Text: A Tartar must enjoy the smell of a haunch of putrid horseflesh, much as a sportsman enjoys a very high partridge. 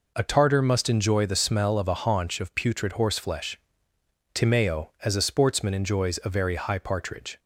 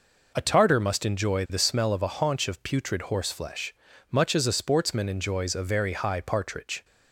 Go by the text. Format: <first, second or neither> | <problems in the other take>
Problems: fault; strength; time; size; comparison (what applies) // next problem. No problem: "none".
second | says "timeo" for "much"; at 4.3 s